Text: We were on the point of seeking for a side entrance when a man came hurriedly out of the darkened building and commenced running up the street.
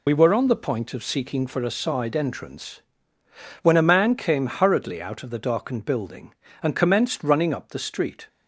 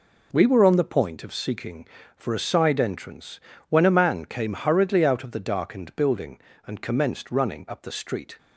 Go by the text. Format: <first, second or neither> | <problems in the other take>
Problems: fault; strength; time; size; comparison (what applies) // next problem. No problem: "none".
second | loses the start of "We"; at 0.0 s; 50 ms // pauses between "entrance" and "when"; noticeable; at 2.8 s; 0.80 s long; slight in the second